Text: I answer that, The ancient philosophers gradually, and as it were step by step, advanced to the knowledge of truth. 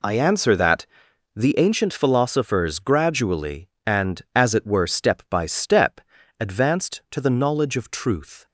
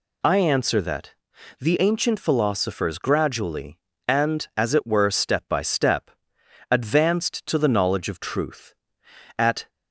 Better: first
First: none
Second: goes on to say "At"; slight; from 9.3 s on; 0.32 s long

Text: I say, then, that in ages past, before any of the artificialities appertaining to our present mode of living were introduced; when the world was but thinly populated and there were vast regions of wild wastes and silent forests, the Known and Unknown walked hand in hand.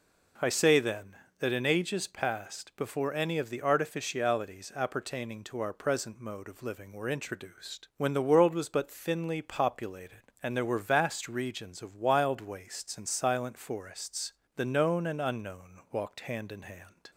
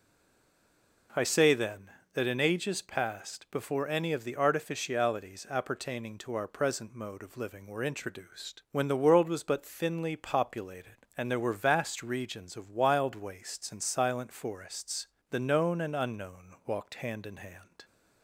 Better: first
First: none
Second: stays silent before the first word; until 1.0 s; 1.0 s long

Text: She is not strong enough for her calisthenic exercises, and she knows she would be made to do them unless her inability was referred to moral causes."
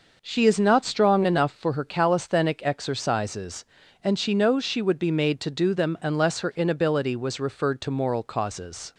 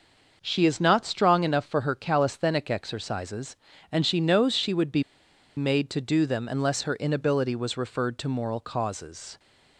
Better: first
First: none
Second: starts louder than the rest; noticeable; until 1.4 s; 6 dB // pauses between "be" and "made"; noticeable; at 5.0 s; 0.54 s long

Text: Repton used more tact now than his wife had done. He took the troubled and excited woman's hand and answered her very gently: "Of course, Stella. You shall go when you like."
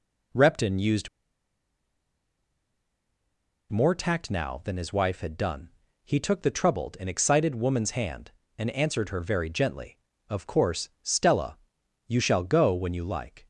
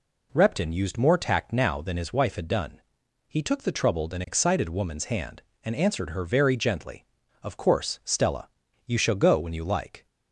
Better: second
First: pauses between "used" and "more"; strong; at 1.0 s; 2.6 s long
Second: none

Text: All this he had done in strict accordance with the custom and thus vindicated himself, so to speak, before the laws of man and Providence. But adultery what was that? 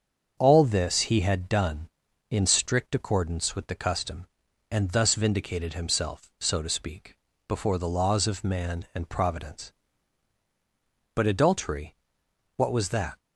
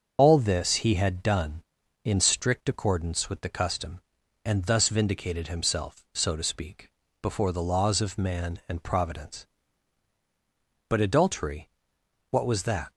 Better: first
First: starts louder than the rest; until 1.3 s; 7 dB // pauses between "adultery" and "what"; noticeable; at 11.9 s; 0.58 s long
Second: loses the start of "All"; at 0.1 s; 65 ms // starts louder than the rest; until 1.1 s; 6.5 dB // pauses between "adultery" and "what"; noticeable; at 11.7 s; 0.58 s long

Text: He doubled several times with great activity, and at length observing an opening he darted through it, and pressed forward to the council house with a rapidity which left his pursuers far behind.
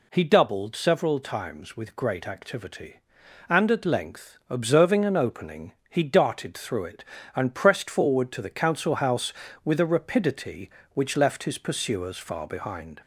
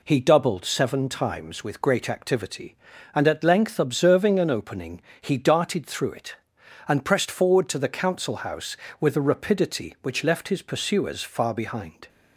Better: first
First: pauses between "opening" and "he"; slight; at 5.7 s; 0.16 s long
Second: says "seven" for "several"; at 0.6 s // pauses between "opening" and "he"; slight; at 5.0 s; 0.20 s long

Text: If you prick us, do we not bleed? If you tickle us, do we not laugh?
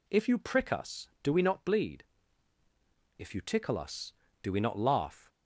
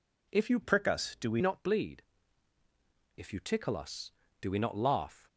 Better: first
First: none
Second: changes voice from "prick" to "we"; from 0.6 to 1.4 s; 0.8 s long

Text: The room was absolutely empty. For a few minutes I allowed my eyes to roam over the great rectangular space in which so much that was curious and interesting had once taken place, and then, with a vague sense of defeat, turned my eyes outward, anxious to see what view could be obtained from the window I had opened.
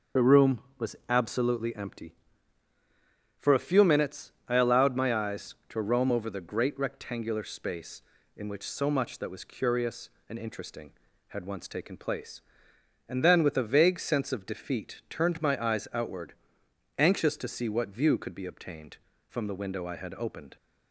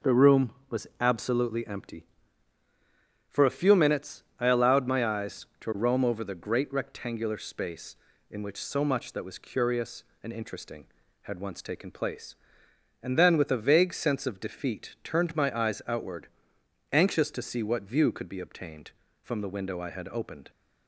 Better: second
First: loses the start of "The"; at 0.1 s; 40 ms // starts louder than the rest; noticeable; until 1.4 s; 6 dB // pauses between "minutes" and "I"; slight; at 4.3 s; 0.16 s long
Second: pauses between "minutes" and "I"; slight; at 4.2 s; 0.16 s long

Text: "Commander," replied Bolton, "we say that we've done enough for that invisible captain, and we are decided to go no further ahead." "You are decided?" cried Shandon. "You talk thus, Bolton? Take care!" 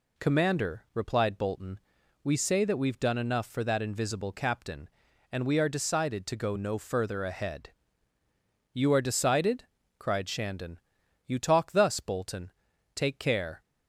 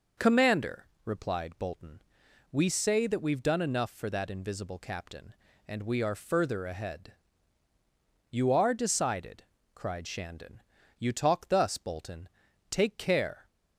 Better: first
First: none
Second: skips "decided to go no"; at 6.1 s

